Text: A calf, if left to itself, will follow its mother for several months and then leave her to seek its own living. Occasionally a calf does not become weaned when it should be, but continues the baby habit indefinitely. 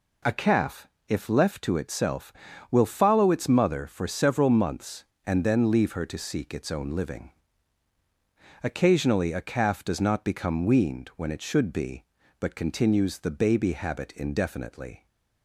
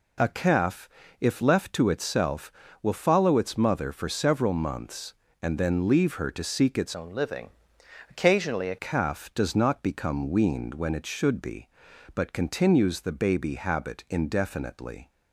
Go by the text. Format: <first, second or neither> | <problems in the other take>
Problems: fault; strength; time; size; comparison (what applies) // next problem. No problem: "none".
first | changes voice from "own" to "a"; from 6.9 to 8.7 s; 1.8 s long